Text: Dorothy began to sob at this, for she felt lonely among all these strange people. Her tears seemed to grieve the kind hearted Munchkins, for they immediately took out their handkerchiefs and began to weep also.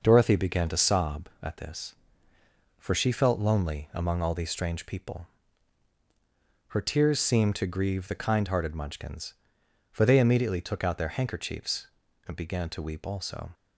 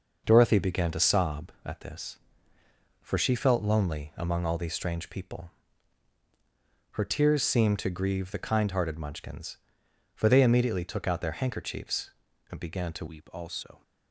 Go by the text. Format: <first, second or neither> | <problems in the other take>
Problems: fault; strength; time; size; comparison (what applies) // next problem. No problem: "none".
first | changes voice at "weep"; from 13.0 s on; 0.8 s long